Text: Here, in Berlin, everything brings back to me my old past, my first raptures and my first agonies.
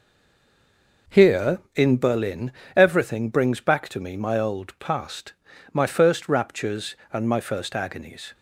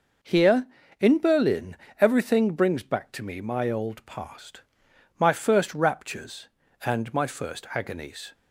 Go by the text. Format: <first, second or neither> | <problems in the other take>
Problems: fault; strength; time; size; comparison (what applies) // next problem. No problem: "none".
second | stays silent before the first word; until 1.0 s; 1.0 s long